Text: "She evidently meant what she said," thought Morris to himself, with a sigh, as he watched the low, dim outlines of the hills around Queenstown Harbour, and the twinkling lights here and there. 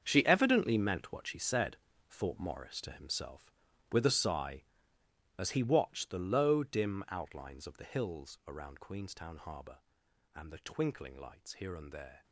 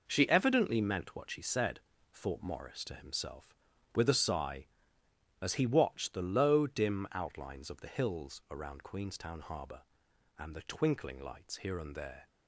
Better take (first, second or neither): second